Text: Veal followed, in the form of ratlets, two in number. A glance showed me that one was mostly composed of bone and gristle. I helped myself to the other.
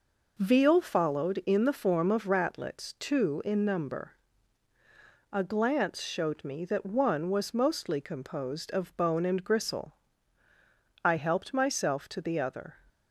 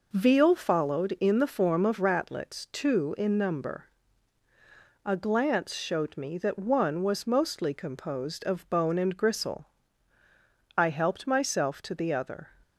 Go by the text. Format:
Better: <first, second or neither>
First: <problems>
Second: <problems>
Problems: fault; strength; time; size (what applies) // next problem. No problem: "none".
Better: neither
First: none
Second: none